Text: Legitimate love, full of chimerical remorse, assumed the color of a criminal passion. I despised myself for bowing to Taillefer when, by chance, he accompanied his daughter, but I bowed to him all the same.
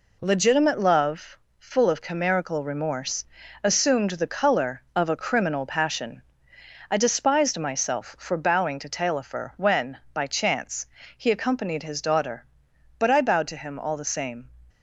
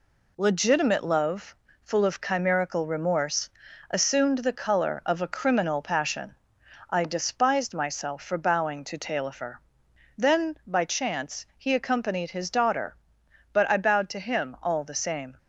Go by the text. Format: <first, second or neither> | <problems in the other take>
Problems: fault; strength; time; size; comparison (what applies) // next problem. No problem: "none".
first | says "then" for "when"; at 10.1 s